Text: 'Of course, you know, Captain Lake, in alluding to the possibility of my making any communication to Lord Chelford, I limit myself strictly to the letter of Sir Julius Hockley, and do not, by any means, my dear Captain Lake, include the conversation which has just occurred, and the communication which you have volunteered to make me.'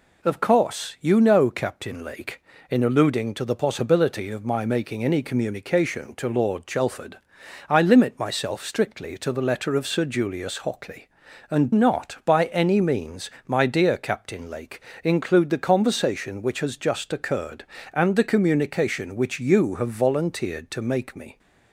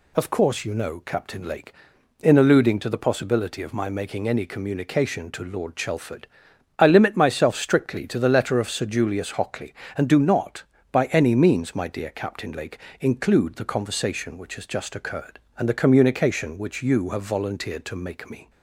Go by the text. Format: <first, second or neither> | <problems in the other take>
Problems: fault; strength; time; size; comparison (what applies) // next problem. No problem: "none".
second | skips "do"; at 11.7 s